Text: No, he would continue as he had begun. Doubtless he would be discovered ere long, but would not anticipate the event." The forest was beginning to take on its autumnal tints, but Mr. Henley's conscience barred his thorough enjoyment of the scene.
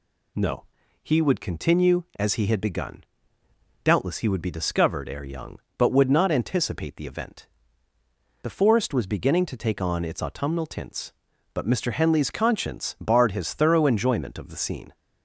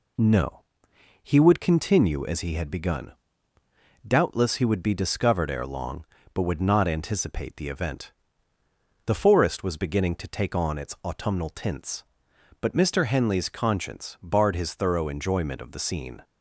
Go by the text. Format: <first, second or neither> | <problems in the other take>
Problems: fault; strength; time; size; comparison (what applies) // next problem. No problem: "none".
second | says "young" for "long"; at 5.2 s